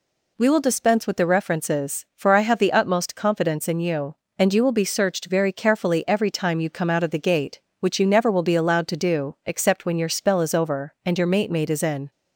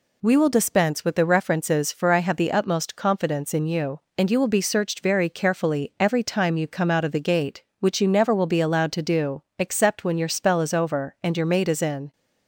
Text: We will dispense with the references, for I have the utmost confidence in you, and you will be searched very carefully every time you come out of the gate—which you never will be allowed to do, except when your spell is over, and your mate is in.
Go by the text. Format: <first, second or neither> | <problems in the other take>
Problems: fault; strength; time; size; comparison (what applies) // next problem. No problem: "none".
second | says "mate" twice; at 11.5 s